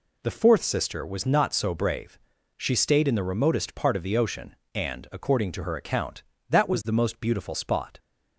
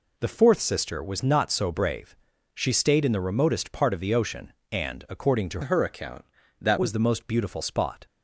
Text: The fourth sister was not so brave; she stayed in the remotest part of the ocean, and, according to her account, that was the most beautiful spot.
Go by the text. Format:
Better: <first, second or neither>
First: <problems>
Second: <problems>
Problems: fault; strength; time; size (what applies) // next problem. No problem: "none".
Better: first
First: none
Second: changes voice from "her" to "that"; from 5.6 to 6.7 s; 1.1 s long